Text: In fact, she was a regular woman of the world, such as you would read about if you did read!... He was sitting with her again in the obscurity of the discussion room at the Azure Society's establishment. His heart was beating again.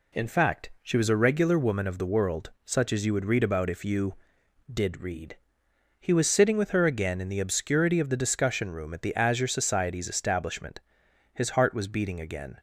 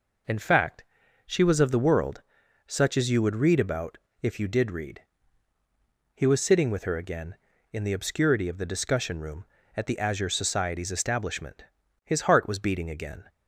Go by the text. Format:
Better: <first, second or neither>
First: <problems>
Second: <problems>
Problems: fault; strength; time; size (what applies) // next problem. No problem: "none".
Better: first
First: none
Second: skips "a regular woman"; at 1.5 s // pauses between "about" and "if"; slight; at 3.9 s; 0.24 s long